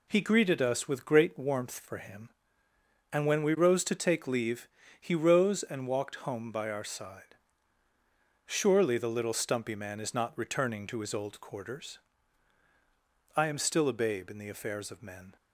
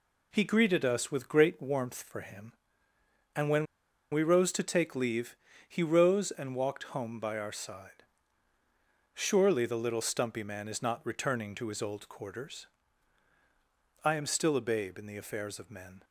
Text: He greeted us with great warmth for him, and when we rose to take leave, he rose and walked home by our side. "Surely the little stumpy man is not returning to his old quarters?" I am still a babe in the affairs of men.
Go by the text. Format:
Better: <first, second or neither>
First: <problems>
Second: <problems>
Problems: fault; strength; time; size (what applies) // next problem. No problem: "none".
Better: first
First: none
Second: pauses between "when" and "we"; noticeable; at 3.6 s; 0.46 s long